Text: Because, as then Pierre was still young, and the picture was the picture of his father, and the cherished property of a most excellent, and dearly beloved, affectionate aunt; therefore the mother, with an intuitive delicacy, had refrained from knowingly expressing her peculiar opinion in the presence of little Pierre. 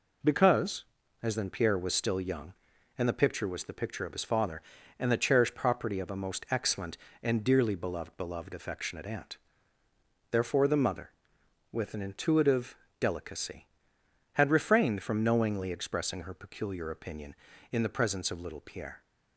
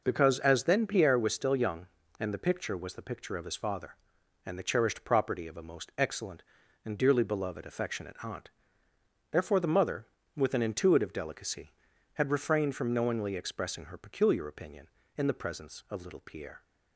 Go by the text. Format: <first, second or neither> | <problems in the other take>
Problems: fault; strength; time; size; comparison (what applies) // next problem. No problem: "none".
second | says "beloved" twice; at 8.1 s // pauses between "intuitive" and "delicacy"; slight; at 12.7 s; 0.22 s long